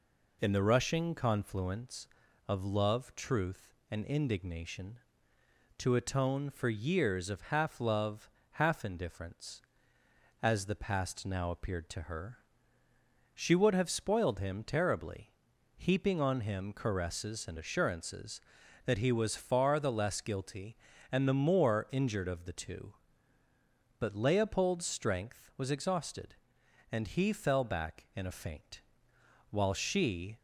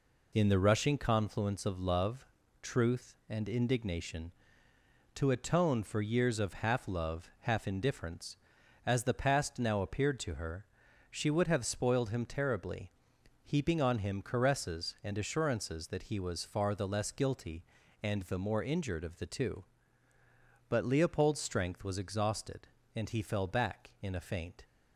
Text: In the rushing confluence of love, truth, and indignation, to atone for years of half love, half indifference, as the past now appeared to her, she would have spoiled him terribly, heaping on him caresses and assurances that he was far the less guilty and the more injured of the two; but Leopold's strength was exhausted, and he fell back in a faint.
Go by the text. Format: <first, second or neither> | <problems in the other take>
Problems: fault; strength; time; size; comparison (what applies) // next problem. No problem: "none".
second | goes on to say "While she"; noticeable; from 29.5 s on; 0.86 s long